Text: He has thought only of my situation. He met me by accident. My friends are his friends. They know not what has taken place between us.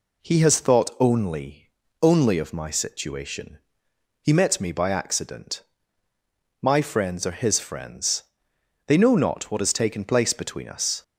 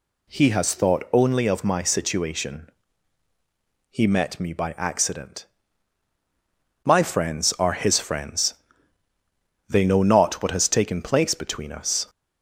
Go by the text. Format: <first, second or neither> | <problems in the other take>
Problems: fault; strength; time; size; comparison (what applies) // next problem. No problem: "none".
second | says "only" twice; at 2.0 s